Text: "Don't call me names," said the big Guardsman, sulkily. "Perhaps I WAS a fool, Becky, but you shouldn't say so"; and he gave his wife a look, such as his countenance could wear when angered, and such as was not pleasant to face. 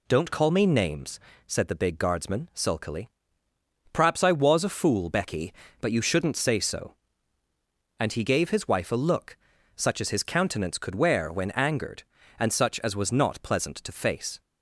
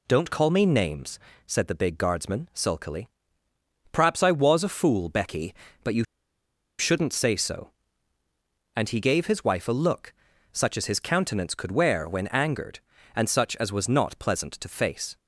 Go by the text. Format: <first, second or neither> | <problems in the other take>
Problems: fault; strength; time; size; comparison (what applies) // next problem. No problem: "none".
first | pauses between "you" and "shouldn't"; noticeable; at 6.0 s; 0.75 s long